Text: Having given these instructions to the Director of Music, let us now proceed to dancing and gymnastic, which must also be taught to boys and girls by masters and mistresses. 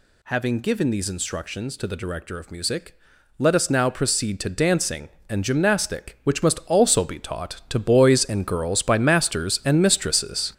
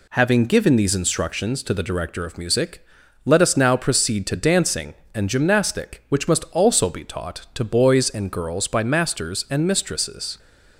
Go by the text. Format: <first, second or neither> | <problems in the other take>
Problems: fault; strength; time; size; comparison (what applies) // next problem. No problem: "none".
second | gets louder; strong; throughout; 8 dB